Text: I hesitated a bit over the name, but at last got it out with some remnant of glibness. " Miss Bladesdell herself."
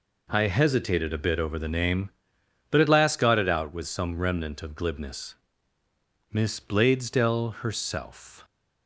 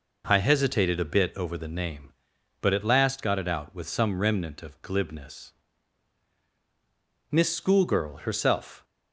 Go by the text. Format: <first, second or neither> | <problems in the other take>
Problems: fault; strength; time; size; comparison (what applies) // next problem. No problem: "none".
first | starts louder than the rest; noticeable; until 1.2 s; 6 dB // says "Schoolgirl" for "Bladesdell"; at 7.5 s